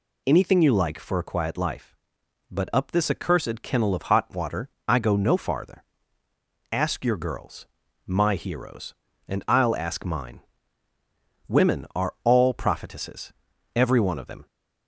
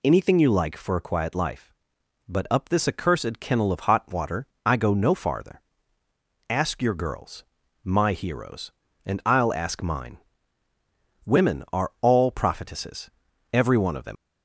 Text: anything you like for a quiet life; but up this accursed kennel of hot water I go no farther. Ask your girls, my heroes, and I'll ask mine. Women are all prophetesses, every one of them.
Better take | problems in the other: first | pauses between "water" and "I"; slight; at 4.4 s; 0.18 s long; slight in the first // leaves "them" unfinished; at 14.1 s; 80 ms

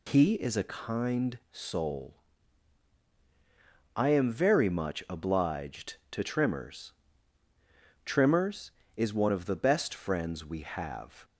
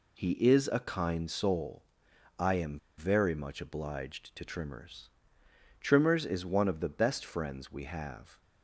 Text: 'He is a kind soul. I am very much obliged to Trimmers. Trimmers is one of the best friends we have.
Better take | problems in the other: first | pauses between "am" and "very"; slight; at 2.7 s; 0.19 s long

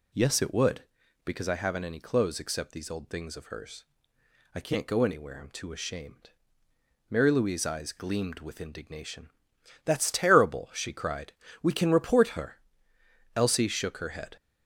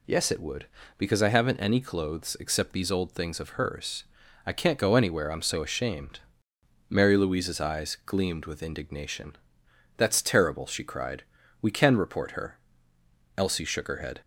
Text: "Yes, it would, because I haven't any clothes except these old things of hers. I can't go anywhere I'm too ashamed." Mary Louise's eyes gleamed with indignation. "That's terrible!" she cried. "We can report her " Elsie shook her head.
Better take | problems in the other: first | says "so" for "too"; at 5.4 s

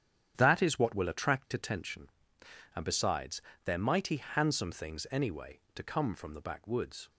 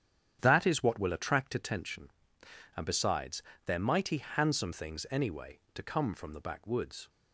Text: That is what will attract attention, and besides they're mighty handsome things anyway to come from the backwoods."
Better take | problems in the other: neither | starts louder than the rest; strong; the same in both // pauses between "besides" and "they're"; slight; the same in both

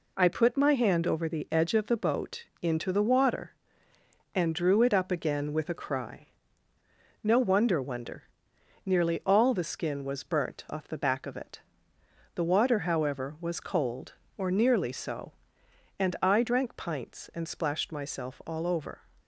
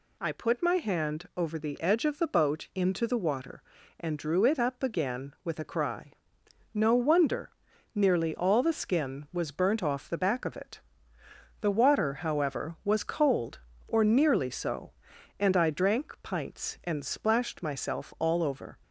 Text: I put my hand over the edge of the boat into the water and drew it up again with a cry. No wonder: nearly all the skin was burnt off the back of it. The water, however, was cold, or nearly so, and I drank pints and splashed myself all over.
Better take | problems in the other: second | pauses between "boat" and "into"; slight; at 2.4 s; 0.16 s long // says "wonder" twice; at 7.7 s

